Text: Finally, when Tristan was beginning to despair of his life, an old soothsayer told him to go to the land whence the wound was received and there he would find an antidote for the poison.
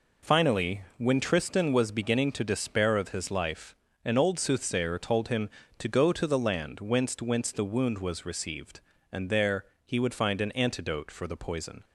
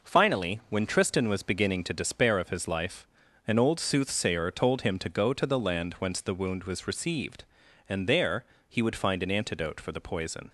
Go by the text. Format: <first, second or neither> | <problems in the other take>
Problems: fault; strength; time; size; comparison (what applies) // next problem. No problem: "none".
second | says "whence" twice; at 7.1 s // pauses between "there" and "he"; slight; at 9.6 s; 0.18 s long; slight in the second